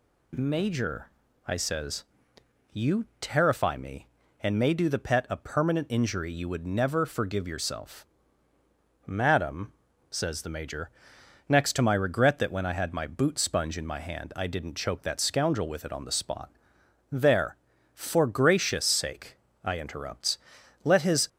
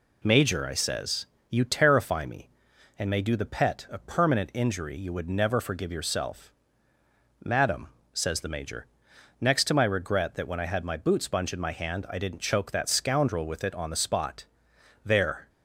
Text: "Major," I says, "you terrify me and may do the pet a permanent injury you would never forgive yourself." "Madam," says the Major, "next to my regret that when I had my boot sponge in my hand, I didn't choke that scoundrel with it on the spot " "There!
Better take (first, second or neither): second